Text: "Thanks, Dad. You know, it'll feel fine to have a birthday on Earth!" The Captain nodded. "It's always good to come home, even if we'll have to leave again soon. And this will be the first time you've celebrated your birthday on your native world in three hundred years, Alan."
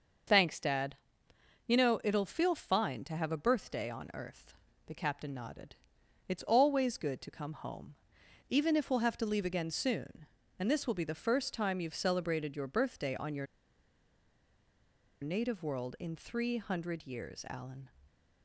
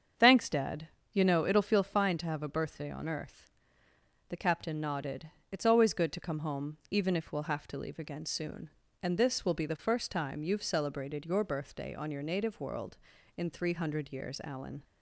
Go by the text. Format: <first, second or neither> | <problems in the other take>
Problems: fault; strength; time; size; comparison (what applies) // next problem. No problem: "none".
second | starts louder than the rest; until 2.0 s; 6 dB; strong in the second // pauses between "your" and "native"; strong; at 13.4 s; 1.7 s long